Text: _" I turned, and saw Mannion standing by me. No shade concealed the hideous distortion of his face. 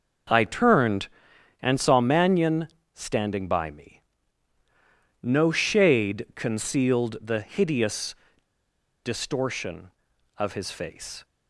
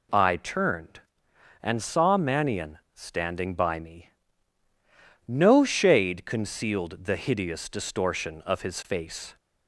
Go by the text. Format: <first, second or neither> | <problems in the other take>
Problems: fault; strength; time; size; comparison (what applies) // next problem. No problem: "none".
second | pauses between "Mannion" and "standing"; slight; at 2.6 s; 0.24 s long // pauses between "hideous" and "distortion"; noticeable; at 8.1 s; 0.88 s long